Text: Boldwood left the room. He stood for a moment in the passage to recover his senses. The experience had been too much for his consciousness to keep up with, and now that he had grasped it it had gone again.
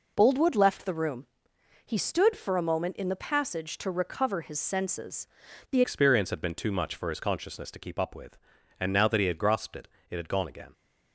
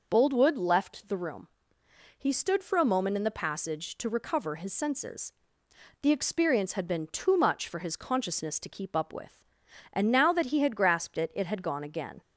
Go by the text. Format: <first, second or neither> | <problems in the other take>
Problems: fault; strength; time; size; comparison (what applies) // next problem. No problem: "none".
second | changes voice at "experience"; from 5.8 s on; 4.9 s long // pauses between "it" and "it"; slight; at 9.8 s; 0.22 s long